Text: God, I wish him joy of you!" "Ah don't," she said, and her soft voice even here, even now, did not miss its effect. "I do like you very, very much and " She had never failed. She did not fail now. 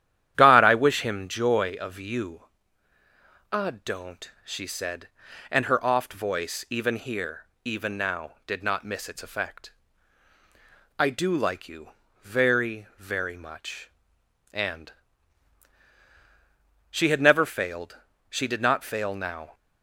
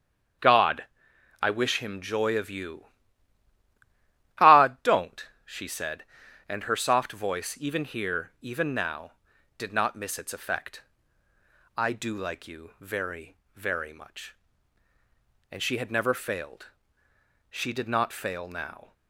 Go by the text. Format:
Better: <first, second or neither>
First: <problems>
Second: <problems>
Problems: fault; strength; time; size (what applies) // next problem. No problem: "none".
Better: second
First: starts louder than the rest; strong; until 1.3 s; 11 dB // says "oft" for "soft"; at 5.8 s // pauses between "you" and "very"; slight; at 11.9 s; 0.30 s long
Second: starts louder than the rest; strong; until 2.0 s; 7.5 dB